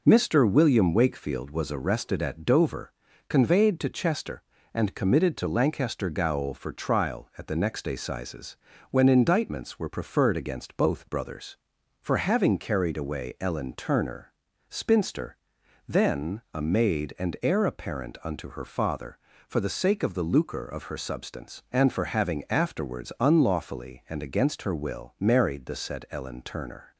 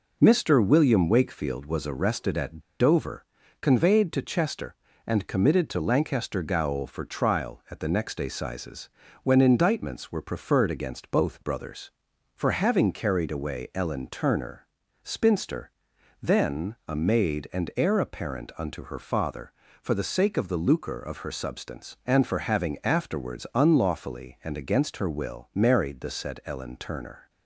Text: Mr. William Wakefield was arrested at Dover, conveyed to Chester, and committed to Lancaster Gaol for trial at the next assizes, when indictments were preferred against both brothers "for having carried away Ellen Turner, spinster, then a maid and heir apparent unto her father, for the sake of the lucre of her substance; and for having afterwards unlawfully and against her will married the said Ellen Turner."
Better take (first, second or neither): first